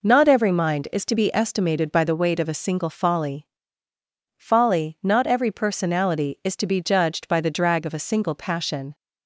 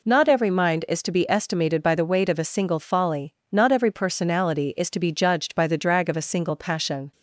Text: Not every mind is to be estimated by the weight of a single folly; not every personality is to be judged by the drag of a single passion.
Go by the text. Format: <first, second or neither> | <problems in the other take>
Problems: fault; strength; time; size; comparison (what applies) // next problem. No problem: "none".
second | says "folly" twice; at 4.3 s